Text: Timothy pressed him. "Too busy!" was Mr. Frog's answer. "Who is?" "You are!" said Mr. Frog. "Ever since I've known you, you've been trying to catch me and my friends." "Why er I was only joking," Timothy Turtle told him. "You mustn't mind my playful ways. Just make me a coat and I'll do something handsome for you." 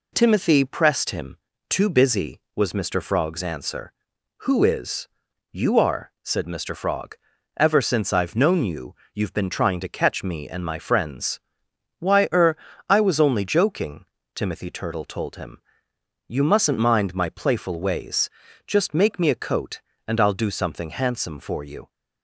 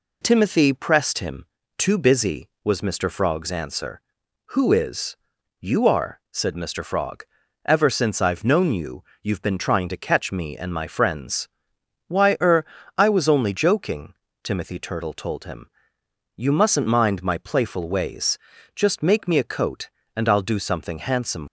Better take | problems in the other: first | pauses between "er" and "I"; slight; at 12.6 s; 0.32 s long; slight in the first // stops before "for you"; at 21.4 s

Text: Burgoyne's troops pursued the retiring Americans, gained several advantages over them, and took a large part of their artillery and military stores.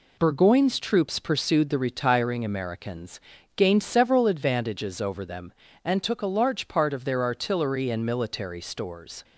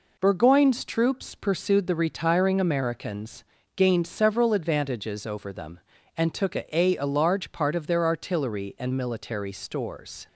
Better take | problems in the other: first | says "a" twice; at 6.7 s

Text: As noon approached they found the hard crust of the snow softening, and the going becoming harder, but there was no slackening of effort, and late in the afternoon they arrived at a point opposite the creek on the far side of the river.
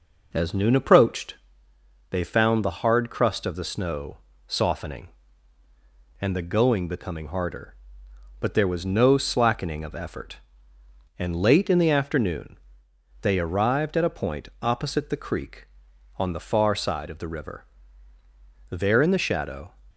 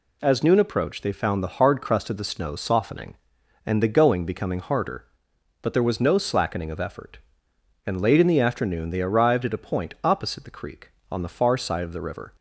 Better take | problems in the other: second | pauses between "approached" and "they"; noticeable; at 1.3 s; 0.74 s long // pauses between "snow" and "softening"; slight; at 4.1 s; 0.30 s long // pauses between "afternoon" and "they"; noticeable; at 12.5 s; 0.64 s long // goes on to say "There in the shadow"; noticeable; from 18.6 s on; 1.0 s long

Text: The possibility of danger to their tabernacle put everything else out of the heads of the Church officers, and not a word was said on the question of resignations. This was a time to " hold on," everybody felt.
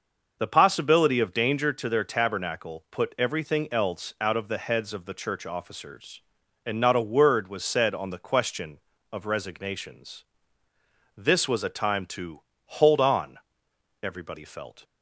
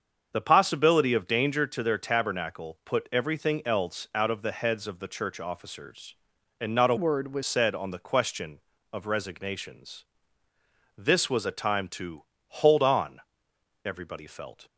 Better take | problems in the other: first | starts louder than the rest; until 1.3 s; 7 dB // changes voice from "word" to "was"; from 6.9 to 7.4 s; 0.5 s long

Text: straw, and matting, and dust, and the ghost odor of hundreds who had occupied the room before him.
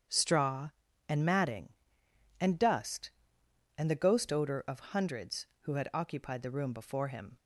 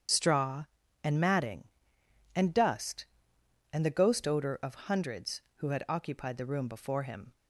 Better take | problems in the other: first | loses the start of "straw"; at 0.0 s; 50 ms // starts louder than the rest; strong; until 1.4 s; 8 dB; strong in the first

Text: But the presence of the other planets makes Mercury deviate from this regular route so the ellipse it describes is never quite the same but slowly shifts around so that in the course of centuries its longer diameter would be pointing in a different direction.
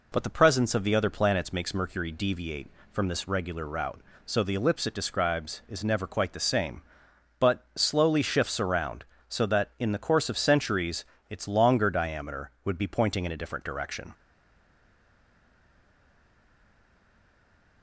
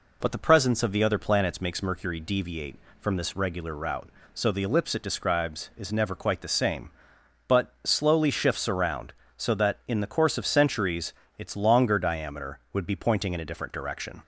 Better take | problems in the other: second | pauses between "centuries" and "its"; slight; at 11.0 s; 0.28 s long; slight in the second // stays silent after the last word; strong; from 14.1 s on; 3.7 s long

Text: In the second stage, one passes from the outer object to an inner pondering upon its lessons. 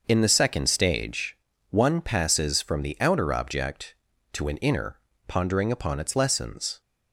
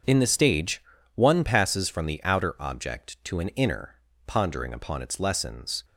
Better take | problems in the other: first | starts louder than the rest; until 1.3 s; 6.5 dB; also in the first // skips "second"; at 0.2 s // pauses between "inner" and "pondering"; slight; at 3.9 s; 0.32 s long; slight in the first

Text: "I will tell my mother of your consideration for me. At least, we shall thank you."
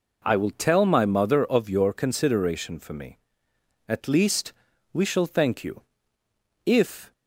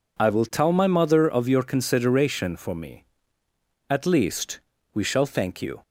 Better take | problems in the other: second | goes on to say "If"; slight; from 6.6 s on; 0.48 s long

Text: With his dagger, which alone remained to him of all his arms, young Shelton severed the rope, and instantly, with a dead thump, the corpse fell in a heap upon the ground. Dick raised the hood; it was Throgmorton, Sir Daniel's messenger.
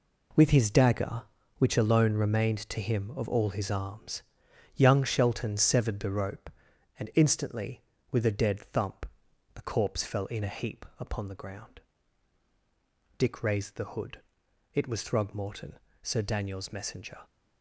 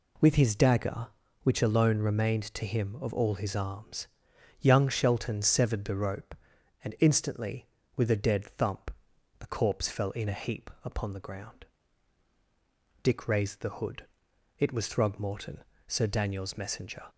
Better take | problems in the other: second | gets quieter; strong; throughout; 9 dB

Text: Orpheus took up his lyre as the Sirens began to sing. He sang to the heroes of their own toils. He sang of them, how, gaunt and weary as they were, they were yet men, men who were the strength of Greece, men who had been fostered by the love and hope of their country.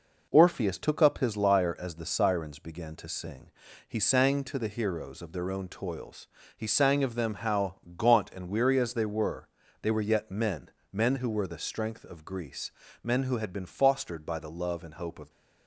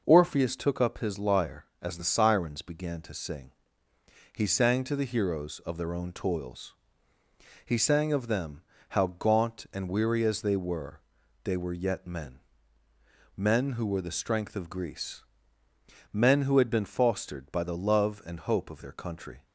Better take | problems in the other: second | stops before "their country"; at 15.2 s

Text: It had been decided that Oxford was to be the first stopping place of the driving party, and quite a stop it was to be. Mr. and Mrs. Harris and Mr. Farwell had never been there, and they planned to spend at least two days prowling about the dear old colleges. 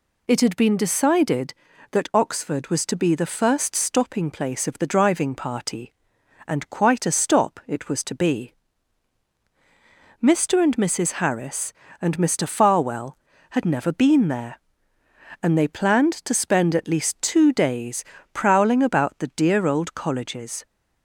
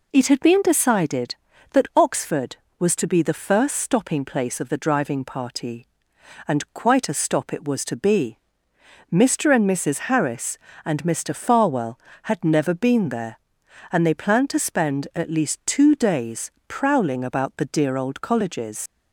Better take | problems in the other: first | pauses between "days" and "prowling"; slight; at 16.4 s; 0.20 s long; slight in the first // leaves "colleges" unfinished; at 18.8 s; 95 ms

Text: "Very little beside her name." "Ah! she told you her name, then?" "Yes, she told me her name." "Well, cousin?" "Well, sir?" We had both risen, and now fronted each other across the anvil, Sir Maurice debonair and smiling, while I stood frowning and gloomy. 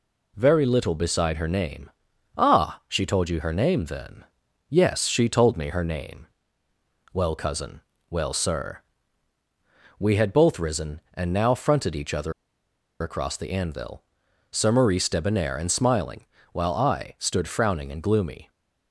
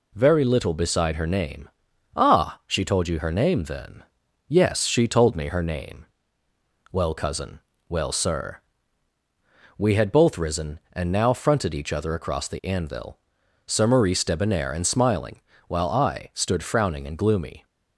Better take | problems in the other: second | pauses between "other" and "across"; noticeable; at 12.3 s; 0.69 s long

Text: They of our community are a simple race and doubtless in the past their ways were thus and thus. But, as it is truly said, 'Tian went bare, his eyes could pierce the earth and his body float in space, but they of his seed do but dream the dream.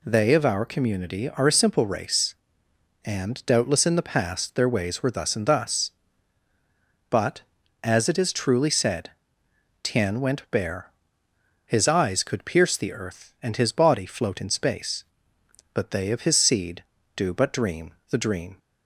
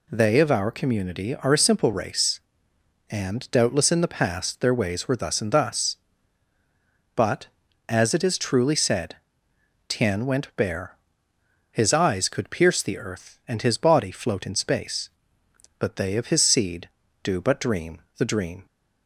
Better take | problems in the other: neither | pauses between "dream" and "the"; slight; the same in both

